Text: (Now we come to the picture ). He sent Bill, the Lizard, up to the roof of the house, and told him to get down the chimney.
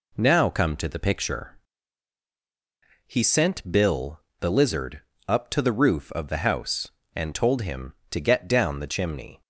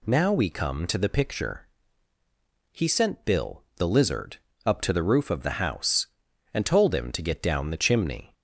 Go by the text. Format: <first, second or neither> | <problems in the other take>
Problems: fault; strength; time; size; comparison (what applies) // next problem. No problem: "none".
second | skips "we"; at 0.4 s